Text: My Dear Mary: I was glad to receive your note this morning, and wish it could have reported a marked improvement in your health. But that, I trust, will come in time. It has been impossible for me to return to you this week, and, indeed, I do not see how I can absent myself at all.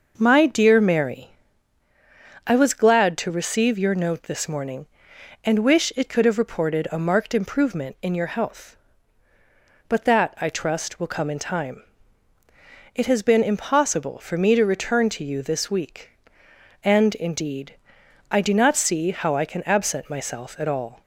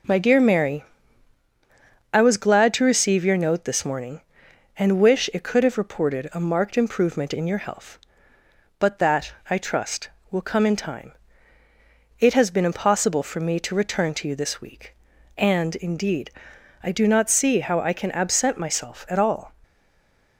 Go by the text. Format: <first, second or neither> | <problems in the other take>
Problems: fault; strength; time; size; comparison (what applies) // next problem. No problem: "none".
first | stays silent after the last word; slight; from 19.6 s on; 0.7 s long